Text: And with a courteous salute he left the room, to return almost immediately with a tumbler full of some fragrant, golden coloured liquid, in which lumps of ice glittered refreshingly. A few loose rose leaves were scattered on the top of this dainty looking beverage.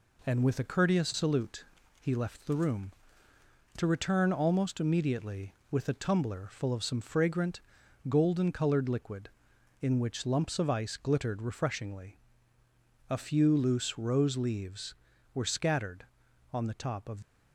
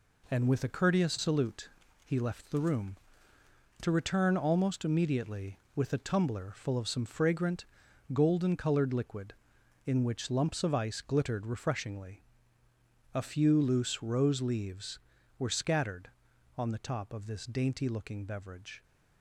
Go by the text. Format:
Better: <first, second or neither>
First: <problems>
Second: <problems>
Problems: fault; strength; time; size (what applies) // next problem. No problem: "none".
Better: second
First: pauses between "salute" and "he"; slight; at 1.6 s; 0.36 s long // stops before "this dainty looking beverage"; at 17.2 s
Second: pauses between "salute" and "he"; slight; at 1.6 s; 0.36 s long